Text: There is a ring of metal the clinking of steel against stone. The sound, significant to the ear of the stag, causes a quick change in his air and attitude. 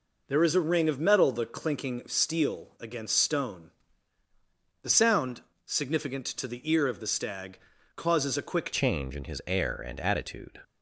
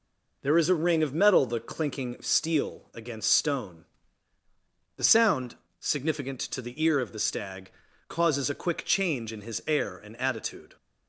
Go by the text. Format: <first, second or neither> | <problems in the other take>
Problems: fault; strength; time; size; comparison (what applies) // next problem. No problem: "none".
second | changes voice at "change"; from 8.7 s on; 1.8 s long